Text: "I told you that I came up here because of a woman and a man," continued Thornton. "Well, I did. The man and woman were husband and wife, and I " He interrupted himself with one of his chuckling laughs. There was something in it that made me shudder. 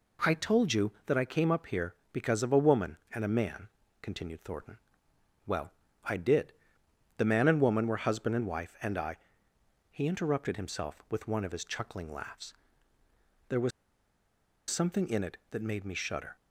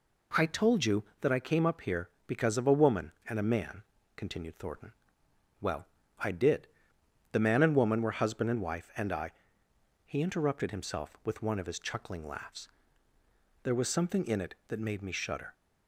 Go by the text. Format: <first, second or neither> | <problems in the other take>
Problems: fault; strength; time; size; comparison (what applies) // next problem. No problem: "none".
second | pauses between "was" and "something"; at 13.7 s; 0.98 s long